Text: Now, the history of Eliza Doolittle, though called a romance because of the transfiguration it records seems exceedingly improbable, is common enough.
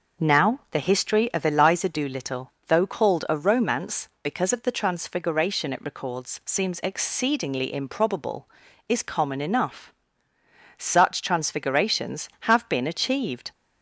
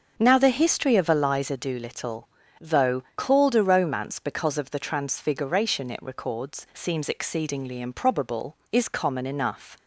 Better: second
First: starts louder than the rest; until 1.3 s; 6 dB // goes on to say "Such transfigurations have been achieved"; strong; from 10.7 s on; 2.7 s long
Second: starts louder than the rest; until 1.1 s; 6.5 dB

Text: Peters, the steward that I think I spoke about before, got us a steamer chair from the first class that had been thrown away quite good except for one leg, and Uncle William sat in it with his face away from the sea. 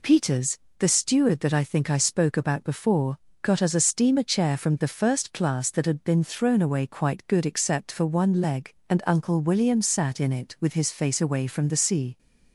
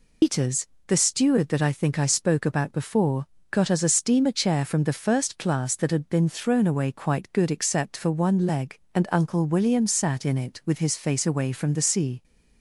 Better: first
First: none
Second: loses the start of "Peters"; at 0.2 s; 105 ms

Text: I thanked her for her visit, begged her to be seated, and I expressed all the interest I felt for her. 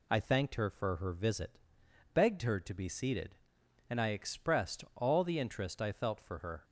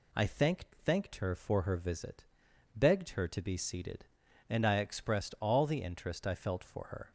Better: first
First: none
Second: says "thanked" twice; at 0.8 s

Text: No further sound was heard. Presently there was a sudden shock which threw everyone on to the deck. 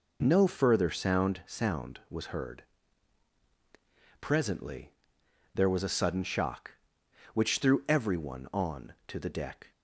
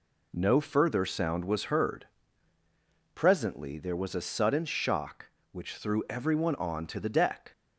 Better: second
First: says "sound" twice; at 1.4 s // pauses between "Presently" and "there"; noticeable; at 4.9 s; 0.64 s long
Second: none

